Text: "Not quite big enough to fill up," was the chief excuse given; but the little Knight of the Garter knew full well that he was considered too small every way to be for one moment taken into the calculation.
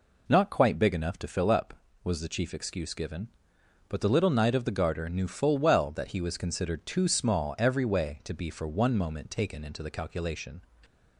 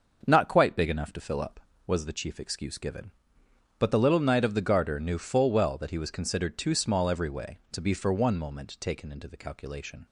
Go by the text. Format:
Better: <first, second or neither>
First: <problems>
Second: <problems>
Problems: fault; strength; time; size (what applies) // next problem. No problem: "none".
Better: first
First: none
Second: starts louder than the rest; until 2.0 s; 6.5 dB